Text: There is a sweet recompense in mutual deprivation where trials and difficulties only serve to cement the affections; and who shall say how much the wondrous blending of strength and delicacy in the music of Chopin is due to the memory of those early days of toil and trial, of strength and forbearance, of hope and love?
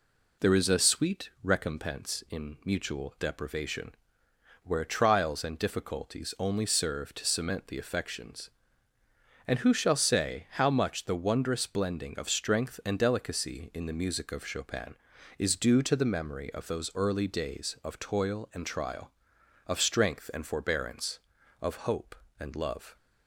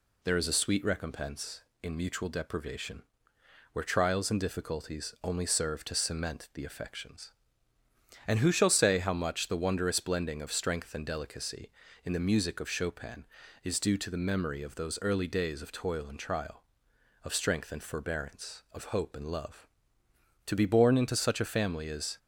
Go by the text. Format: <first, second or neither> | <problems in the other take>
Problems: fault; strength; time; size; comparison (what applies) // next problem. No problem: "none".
first | pauses between "deprivation" and "where"; noticeable; at 3.0 s; 0.68 s long; noticeable in the first // goes on to say "To be born into such a family is"; strong; from 20.4 s on; 1.7 s long